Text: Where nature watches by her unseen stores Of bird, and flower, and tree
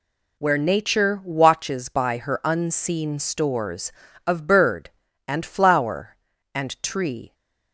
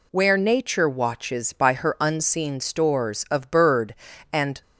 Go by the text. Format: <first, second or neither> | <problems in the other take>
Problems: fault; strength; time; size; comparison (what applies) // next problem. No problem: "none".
first | stops before "flower and tree"; at 4.6 s